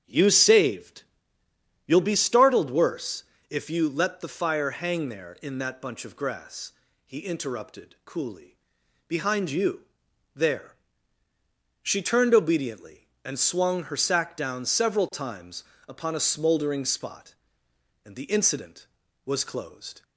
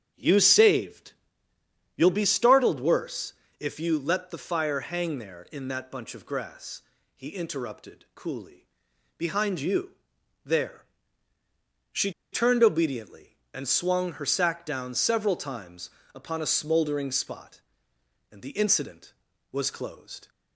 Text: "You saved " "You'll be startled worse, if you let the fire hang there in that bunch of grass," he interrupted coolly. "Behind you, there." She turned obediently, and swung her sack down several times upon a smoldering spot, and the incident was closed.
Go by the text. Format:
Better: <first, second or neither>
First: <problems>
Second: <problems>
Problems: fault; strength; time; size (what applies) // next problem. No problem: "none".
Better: first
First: starts louder than the rest; strong; until 1.4 s; 8.5 dB // pauses between "times" and "upon"; slight; at 15.6 s; 0.24 s long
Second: starts louder than the rest; strong; until 1.5 s; 8.5 dB // pauses between "She" and "turned"; slight; at 12.1 s; 0.20 s long // pauses between "times" and "upon"; slight; at 15.9 s; 0.24 s long